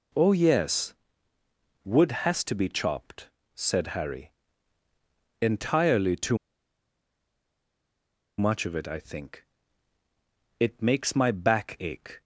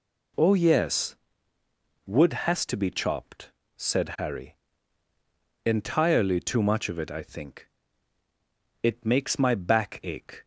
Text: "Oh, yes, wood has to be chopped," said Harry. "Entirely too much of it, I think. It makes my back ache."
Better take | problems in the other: second | pauses between "too" and "much"; strong; at 6.3 s; 2.0 s long

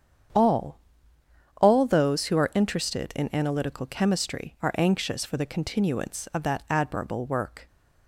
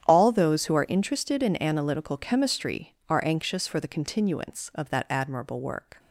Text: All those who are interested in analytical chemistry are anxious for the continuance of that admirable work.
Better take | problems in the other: second | starts louder than the rest; strong; until 2.1 s; 8.5 dB; strong in the second // says "All" twice; at 1.5 s

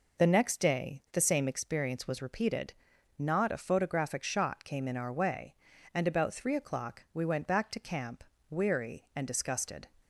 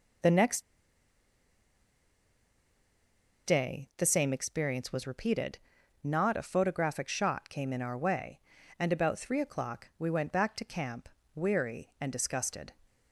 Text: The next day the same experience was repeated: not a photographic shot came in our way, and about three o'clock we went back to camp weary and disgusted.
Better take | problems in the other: first | pauses between "next" and "day"; strong; at 0.6 s; 2.8 s long // pauses between "camp" and "weary"; slight; at 11.0 s; 0.26 s long; slight in the first

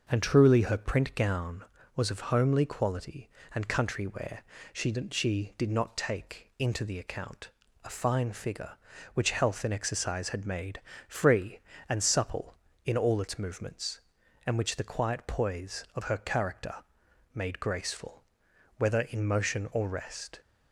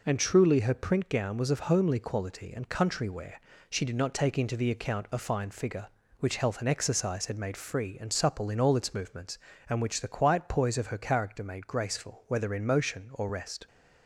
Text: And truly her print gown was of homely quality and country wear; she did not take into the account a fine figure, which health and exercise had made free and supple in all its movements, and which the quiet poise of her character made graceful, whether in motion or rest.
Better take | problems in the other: second | says "she" twice; at 5.0 s // pauses between "account" and "a"; slight; at 7.4 s; 0.34 s long // pauses between "made" and "free"; slight; at 10.7 s; 0.30 s long // pauses between "character" and "made"; noticeable; at 16.7 s; 0.58 s long

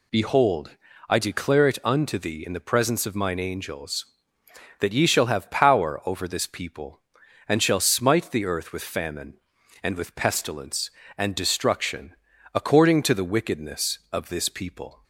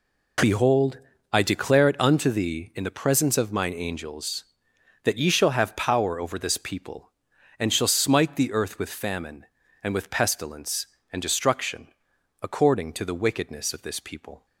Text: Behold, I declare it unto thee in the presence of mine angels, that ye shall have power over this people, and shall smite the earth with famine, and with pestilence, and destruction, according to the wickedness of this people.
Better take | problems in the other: neither | none

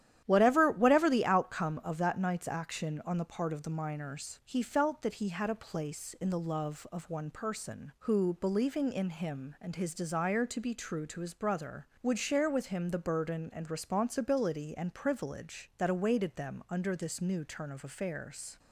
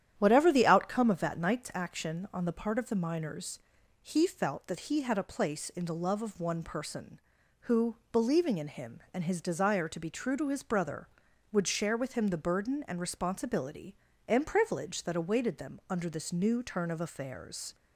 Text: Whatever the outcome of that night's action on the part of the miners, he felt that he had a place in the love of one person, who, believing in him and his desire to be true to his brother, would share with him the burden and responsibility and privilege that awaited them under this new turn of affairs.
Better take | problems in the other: second | starts louder than the rest; strong; until 1.2 s; 11.5 dB; strong in the second // says "Whatever" twice; at 0.7 s

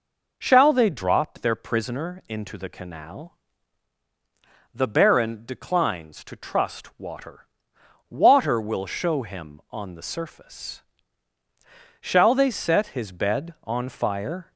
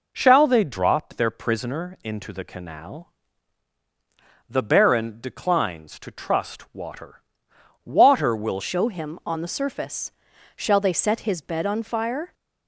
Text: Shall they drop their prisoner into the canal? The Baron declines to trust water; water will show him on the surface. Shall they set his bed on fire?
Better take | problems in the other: first | changes voice at "show"; from 8.5 s on; 3.8 s long

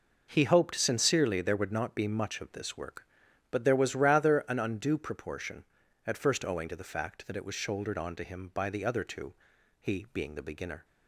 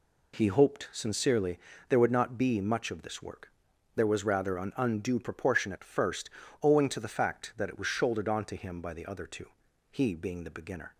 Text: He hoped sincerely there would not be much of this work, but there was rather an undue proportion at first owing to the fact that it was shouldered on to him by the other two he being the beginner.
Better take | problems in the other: first | pauses between "sincerely" and "there"; slight; at 1.6 s; 0.26 s long // skips "but"; at 3.7 s // pauses between "first" and "owing"; slight; at 6.2 s; 0.32 s long // pauses between "two" and "he"; at 9.4 s; 0.42 s long; noticeable in the first

